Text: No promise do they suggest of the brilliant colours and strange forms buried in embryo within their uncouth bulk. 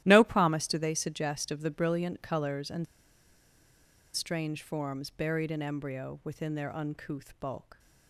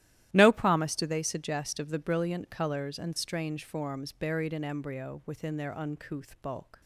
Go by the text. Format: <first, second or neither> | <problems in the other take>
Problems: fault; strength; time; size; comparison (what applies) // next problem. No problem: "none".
second | starts louder than the rest; strong; until 1.0 s; 13.5 dB; strong in the second // pauses between "and" and "strange"; strong; at 2.8 s; 1.3 s long